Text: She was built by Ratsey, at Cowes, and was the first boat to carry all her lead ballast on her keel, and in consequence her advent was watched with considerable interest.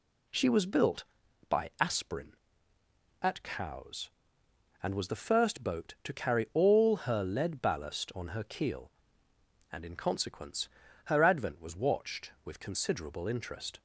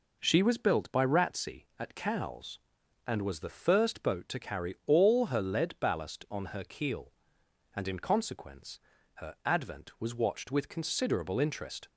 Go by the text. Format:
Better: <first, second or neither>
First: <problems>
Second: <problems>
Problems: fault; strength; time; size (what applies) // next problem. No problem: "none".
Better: second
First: says "Aspirin" for "Ratsey"; at 1.7 s // pauses between "consequence" and "her"; at 10.6 s; 0.38 s long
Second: pauses between "consequence" and "her"; slight; at 8.7 s; 0.36 s long